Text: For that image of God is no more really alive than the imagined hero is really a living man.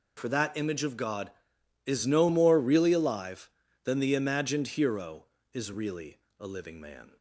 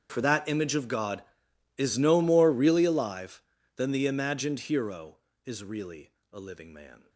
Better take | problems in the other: first | gets quieter; strong; throughout; 22.5 dB // pauses between "really" and "a"; slight; at 6.0 s; 0.22 s long; slight in the first

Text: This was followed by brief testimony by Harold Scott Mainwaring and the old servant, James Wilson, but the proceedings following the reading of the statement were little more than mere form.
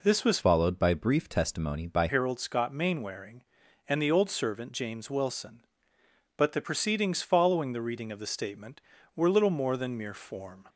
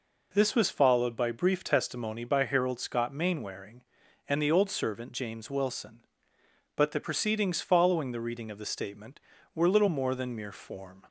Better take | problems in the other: second | changes voice from "followed" to "by"; from 0.4 to 2.0 s; 1.6 s long

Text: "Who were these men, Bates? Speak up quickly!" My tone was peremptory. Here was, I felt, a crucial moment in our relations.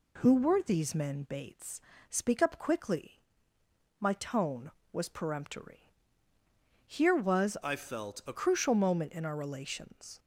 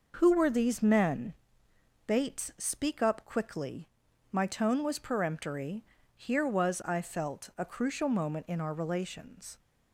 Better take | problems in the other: second | changes voice from "I" to "a"; from 7.6 to 8.3 s; 0.7 s long

